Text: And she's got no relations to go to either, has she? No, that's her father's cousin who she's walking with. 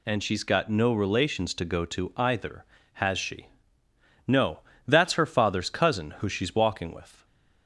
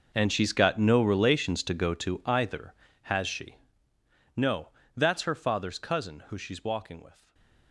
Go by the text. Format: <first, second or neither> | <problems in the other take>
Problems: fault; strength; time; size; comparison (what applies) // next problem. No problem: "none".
first | gets quieter; strong; throughout; 18 dB // stays silent after the last word; slight; from 7.1 s on; 0.6 s long; slight in the first